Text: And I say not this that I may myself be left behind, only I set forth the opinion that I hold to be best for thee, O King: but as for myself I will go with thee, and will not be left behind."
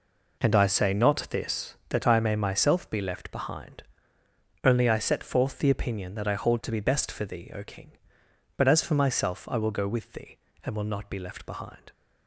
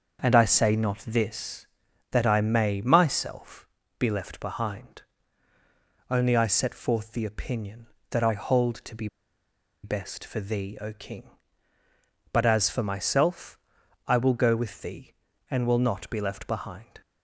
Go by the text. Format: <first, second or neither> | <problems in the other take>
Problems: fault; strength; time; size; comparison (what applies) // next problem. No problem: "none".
first | starts louder than the rest; until 1.3 s; 6.5 dB // pauses between "myself" and "be"; slight; at 3.6 s; 0.32 s long // pauses between "be" and "best"; noticeable; at 9.0 s; 0.77 s long // pauses between "myself" and "I"; noticeable; at 13.5 s; 0.48 s long